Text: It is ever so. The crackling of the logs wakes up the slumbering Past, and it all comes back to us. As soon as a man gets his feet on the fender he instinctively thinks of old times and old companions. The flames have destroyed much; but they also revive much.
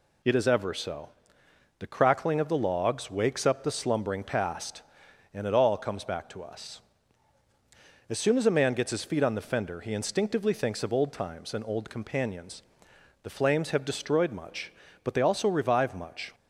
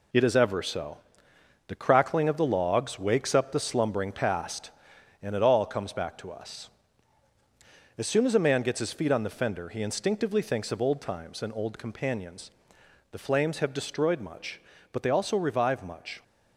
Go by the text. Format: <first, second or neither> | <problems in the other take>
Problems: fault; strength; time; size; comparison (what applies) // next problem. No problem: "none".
first | gets quieter; throughout; 6.5 dB